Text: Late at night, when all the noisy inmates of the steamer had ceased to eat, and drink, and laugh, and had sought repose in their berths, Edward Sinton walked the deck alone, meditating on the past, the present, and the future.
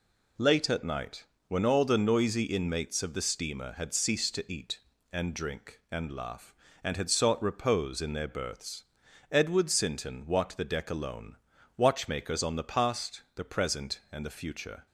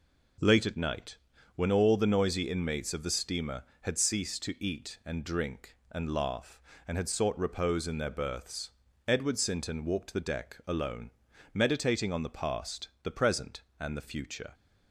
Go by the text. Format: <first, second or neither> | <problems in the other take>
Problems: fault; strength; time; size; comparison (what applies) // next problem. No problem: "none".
second | says "watchmakers" for "meditating"; at 11.7 s